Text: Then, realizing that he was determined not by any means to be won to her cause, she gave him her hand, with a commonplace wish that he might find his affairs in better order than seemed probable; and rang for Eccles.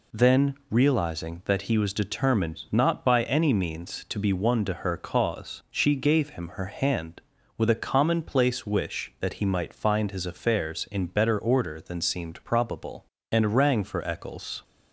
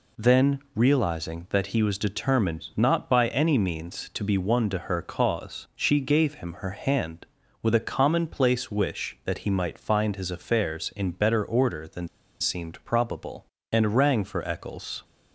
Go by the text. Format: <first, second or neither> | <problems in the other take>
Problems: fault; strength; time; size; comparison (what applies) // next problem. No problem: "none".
first | pauses between "than" and "seemed"; slight; at 12.0 s; 0.33 s long